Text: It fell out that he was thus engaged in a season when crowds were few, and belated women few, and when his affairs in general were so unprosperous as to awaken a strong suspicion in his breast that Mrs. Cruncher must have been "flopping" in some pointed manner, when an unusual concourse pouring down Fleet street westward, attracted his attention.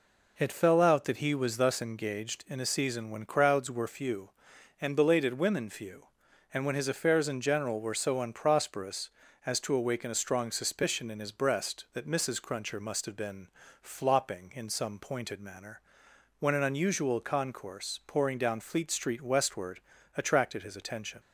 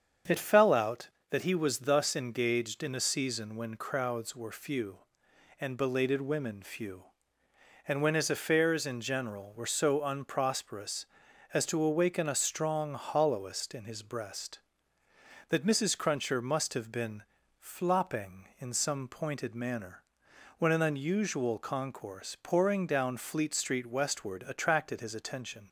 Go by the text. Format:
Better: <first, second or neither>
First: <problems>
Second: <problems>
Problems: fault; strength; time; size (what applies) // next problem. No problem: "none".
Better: first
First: pauses between "been" and "flopping"; slight; at 13.4 s; 0.32 s long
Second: starts louder than the rest; until 1.5 s; 7 dB // says "hollowest" for "suspicion"; at 12.9 s // pauses between "been" and "flopping"; at 17.2 s; 0.38 s long